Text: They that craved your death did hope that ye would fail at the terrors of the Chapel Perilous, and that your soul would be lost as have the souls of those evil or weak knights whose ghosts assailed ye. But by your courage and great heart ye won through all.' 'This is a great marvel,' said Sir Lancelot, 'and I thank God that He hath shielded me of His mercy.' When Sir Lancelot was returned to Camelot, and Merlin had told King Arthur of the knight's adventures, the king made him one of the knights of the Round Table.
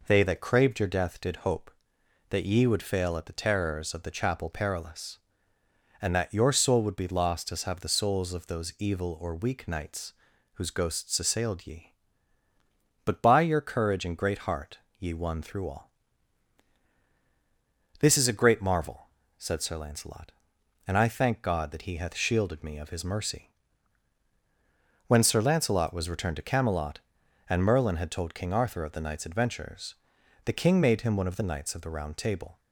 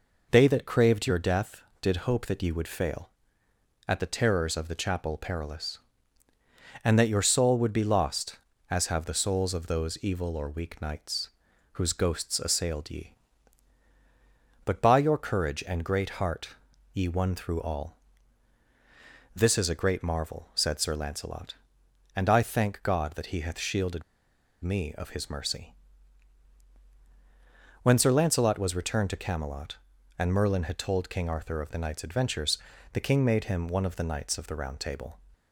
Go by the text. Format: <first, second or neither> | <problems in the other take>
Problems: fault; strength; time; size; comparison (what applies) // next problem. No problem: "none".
first | pauses between "knights" and "whose"; noticeable; at 11.2 s; 0.46 s long; also in the first // pauses between "heart" and "ye"; at 16.4 s; 0.44 s long; slight in the first // pauses between "shielded" and "me"; noticeable; at 24.0 s; 0.59 s long